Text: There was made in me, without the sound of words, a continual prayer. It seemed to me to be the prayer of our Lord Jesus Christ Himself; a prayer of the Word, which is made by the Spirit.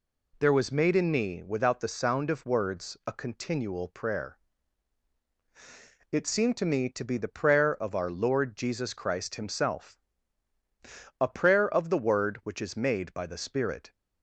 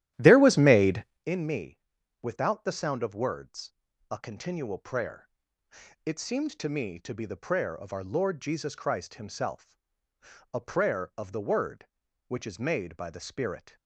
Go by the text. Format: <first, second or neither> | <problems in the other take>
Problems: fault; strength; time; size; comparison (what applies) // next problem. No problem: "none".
first | starts louder than the rest; strong; until 1.3 s; 13 dB